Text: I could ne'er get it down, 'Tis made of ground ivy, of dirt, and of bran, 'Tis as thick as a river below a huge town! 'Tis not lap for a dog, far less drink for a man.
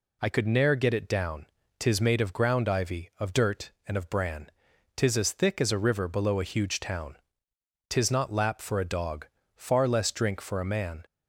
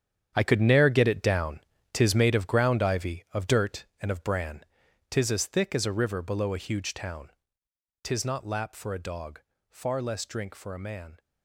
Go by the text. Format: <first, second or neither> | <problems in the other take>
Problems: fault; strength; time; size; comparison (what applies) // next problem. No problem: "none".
first | gets quieter; strong; throughout; 12.5 dB